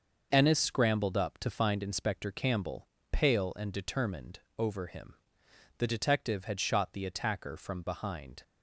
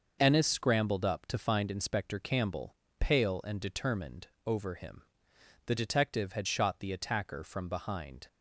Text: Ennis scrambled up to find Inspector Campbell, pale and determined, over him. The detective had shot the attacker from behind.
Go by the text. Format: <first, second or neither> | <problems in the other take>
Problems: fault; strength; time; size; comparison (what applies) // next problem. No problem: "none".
neither | starts louder than the rest; noticeable; the same in both